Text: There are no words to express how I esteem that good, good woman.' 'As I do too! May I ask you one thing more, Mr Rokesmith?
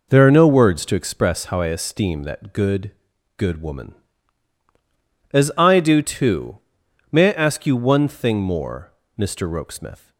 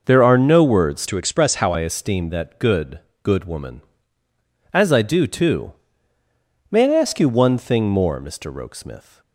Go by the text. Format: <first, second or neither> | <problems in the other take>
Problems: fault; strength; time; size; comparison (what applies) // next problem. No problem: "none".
first | changes voice from "to" to "how"; from 1.0 to 1.7 s; 0.7 s long